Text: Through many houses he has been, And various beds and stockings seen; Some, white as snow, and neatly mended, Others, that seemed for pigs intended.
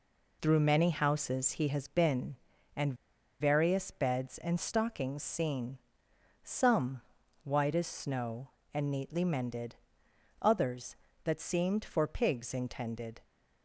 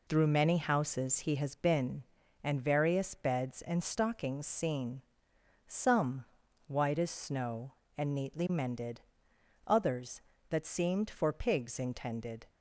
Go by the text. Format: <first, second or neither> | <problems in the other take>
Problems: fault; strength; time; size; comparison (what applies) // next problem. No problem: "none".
second | pauses between "And" and "various"; noticeable; at 2.9 s; 0.46 s long